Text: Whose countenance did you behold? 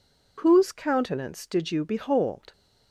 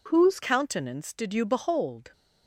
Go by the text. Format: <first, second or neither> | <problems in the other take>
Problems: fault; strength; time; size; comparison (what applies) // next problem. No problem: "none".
first | changes voice at "countenance"; from 0.4 s on; 1.7 s long